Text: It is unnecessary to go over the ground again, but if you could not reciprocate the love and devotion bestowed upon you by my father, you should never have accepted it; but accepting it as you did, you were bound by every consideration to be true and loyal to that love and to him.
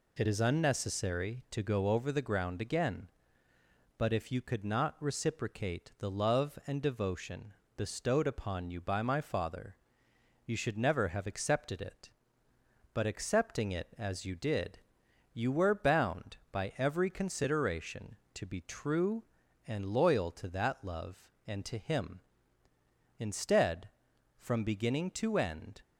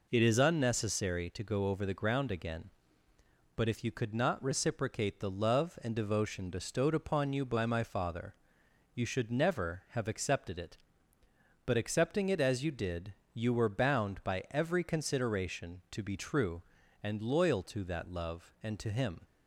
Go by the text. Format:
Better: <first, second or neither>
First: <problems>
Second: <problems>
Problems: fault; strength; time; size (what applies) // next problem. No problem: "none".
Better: second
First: pauses between "devotion" and "bestowed"; slight; at 7.5 s; 0.24 s long // goes on to say "Instead from beginning to end"; strong; from 23.1 s on; 2.6 s long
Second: none